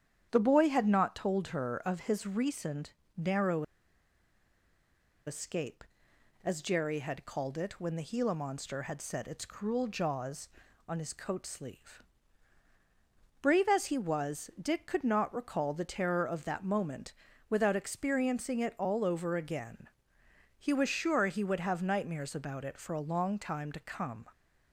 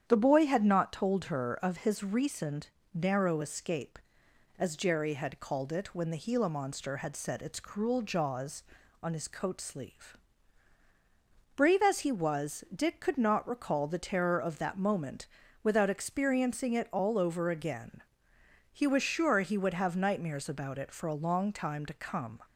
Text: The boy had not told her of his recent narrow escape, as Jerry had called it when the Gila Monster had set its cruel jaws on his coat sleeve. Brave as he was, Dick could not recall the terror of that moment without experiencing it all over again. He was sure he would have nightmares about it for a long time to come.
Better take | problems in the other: second | starts louder than the rest; strong; until 1.3 s; 9 dB; strong in the second // pauses between "recent" and "narrow"; slight; at 2.9 s; 0.24 s long; slight in the second // pauses between "narrow" and "escape"; strong; at 3.6 s; 1.6 s long // pauses between "moment" and "without"; at 17.1 s; 0.38 s long; also in the second

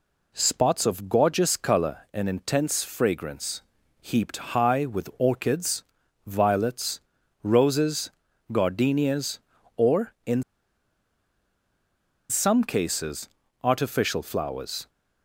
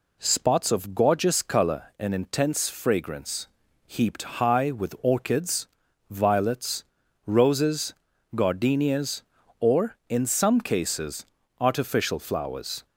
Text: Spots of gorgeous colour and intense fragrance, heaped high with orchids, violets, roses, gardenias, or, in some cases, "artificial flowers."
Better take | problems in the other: second | pauses between "heaped" and "high"; slight; at 4.3 s; 0.18 s long; slight in the second // pauses between "in" and "some"; strong; at 10.4 s; 1.8 s long

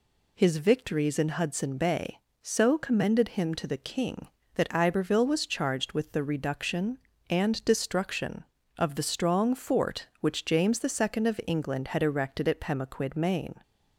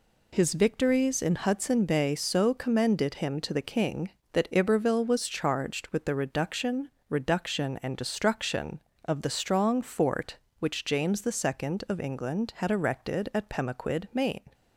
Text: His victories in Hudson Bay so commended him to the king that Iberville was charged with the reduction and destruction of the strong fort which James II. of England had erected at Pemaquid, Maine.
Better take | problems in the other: first | says "reduction" twice; at 7.0 s

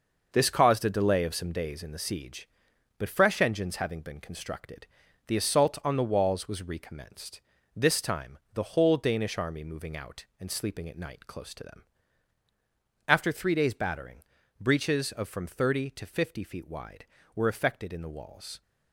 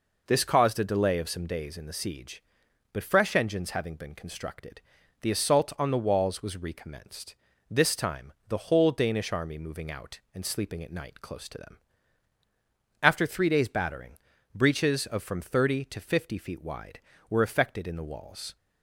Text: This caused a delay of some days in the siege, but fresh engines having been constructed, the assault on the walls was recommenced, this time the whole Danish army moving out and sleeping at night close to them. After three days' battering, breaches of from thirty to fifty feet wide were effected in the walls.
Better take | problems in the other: second | gets quieter; strong; throughout; 7.5 dB // pauses between "time" and "the"; slight; at 8.3 s; 0.16 s long; slight in the second

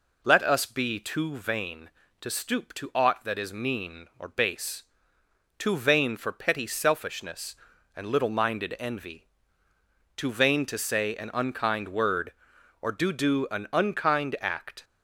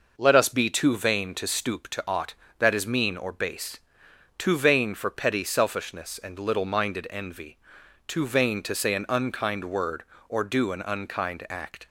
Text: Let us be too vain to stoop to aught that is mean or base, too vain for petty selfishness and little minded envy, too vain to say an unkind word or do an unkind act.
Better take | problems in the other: second | says "do" twice; at 13.1 s

